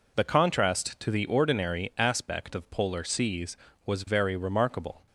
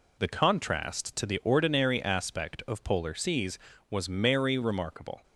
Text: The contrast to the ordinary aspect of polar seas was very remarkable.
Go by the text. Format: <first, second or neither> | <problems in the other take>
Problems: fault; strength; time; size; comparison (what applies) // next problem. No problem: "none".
first | says "merry" for "very"; at 4.0 s